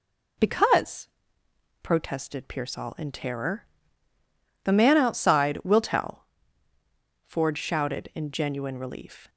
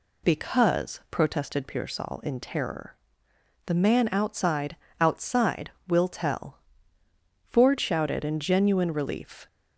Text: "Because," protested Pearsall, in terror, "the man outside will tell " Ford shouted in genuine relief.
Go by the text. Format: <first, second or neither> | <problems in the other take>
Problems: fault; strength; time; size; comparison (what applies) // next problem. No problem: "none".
first | says "outside" twice; at 4.9 s